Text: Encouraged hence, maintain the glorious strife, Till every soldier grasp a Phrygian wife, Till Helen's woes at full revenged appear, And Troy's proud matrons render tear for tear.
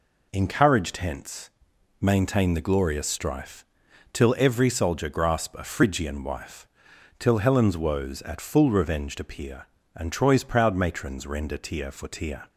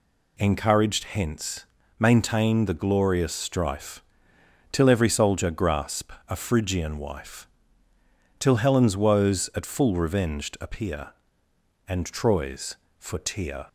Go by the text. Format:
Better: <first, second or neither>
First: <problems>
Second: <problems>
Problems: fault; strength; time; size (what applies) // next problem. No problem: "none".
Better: first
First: none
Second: pauses between "grasp" and "a"; slight; at 6.1 s; 0.16 s long // skips "proud matrons render tear"; at 12.8 s